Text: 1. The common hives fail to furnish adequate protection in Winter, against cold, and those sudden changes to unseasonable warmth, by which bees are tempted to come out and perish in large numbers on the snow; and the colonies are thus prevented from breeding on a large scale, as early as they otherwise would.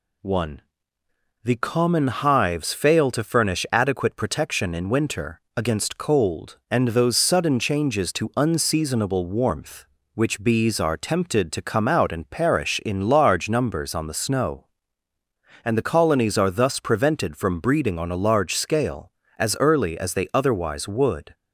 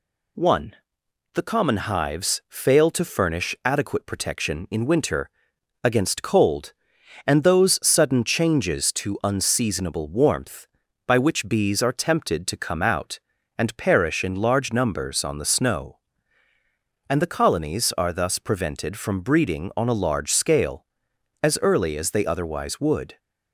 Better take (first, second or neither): second